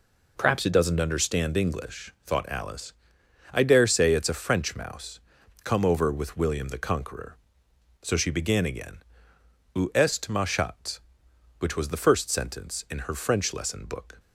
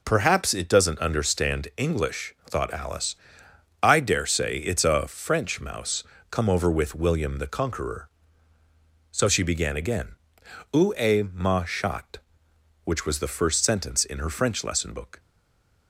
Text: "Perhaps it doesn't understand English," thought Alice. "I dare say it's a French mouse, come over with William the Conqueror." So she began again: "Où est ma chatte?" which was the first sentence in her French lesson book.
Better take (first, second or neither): first